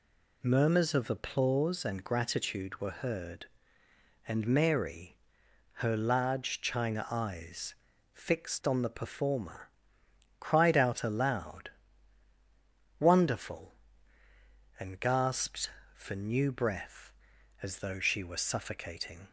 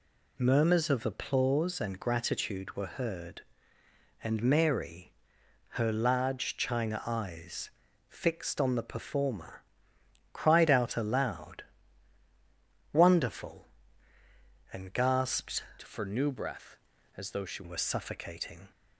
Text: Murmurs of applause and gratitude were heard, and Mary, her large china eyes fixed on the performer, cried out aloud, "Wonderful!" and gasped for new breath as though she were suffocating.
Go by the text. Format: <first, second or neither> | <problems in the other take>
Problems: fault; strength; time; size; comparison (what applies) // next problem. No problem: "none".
first | pauses between "eyes" and "fixed"; at 7.6 s; 0.40 s long; also in the first // changes voice from "for" to "she"; from 15.8 to 17.6 s; 1.8 s long